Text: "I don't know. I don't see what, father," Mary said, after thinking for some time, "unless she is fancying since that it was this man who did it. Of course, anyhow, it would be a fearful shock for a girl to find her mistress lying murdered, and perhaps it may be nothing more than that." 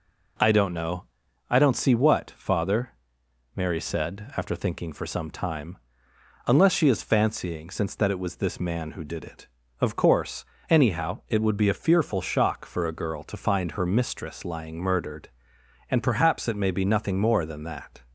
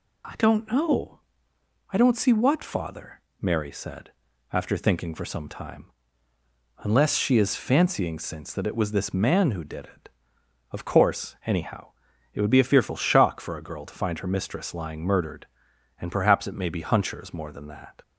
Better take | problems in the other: first | says "hunchers" for "nothing"; at 16.8 s

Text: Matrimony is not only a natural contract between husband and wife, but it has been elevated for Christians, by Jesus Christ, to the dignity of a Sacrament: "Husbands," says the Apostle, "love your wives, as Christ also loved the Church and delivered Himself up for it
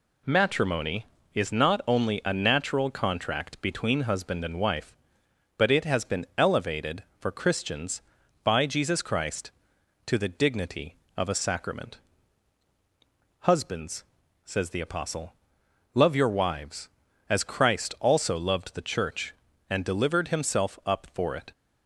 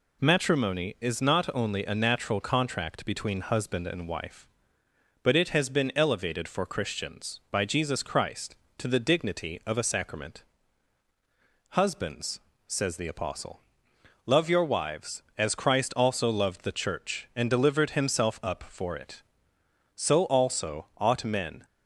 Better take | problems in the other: first | goes on to say "so also ought men"; strong; from 19.9 s on; 1.7 s long

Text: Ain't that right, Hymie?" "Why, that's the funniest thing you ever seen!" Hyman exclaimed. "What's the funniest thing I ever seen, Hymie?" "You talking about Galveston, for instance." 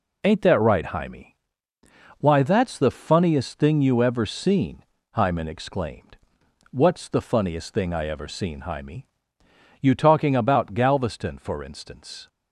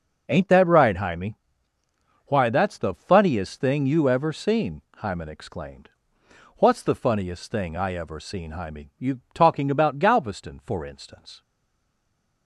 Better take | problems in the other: first | stays silent after the last word; from 11.4 s on; 1.0 s long

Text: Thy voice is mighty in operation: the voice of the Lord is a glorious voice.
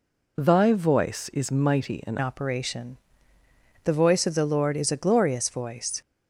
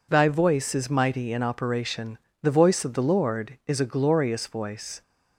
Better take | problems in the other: second | changes voice at "operation"; from 2.2 s on; 3.8 s long

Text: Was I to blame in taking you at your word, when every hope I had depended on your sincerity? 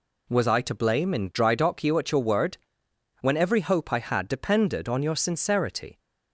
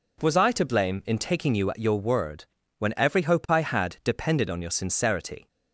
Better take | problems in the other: second | says "drydock" for "taking"; at 1.3 s

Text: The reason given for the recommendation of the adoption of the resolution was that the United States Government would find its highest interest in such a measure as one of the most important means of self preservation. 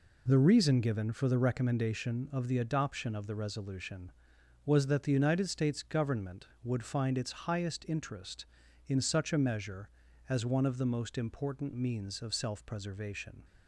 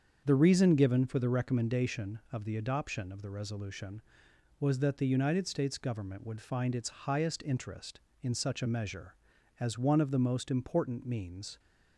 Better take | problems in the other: first | starts louder than the rest; strong; until 1.2 s; 7.5 dB // stops before "of self preservation"; at 11.5 s

